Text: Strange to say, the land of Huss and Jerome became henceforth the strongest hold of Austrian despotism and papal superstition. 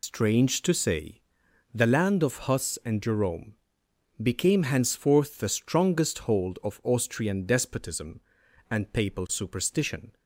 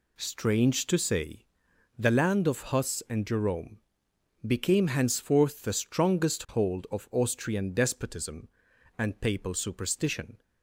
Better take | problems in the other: second | loses the start of "Strange"; at 0.0 s; 95 ms // pauses between "Jerome" and "became"; noticeable; at 3.5 s; 0.66 s long; noticeable in the second

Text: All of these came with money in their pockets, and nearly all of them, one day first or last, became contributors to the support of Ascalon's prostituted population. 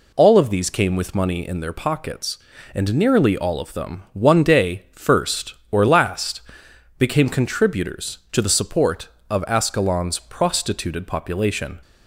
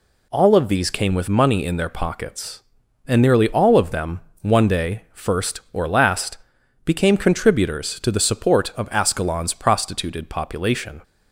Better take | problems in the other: neither | none

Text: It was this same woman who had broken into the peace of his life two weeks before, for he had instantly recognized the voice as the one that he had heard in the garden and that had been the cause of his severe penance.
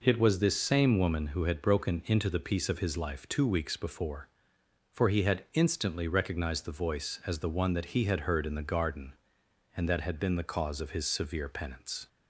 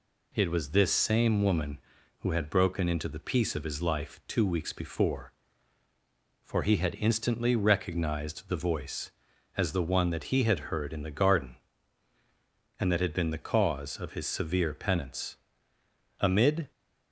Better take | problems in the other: first | goes on to say "Amid"; from 16.1 s on; 0.52 s long

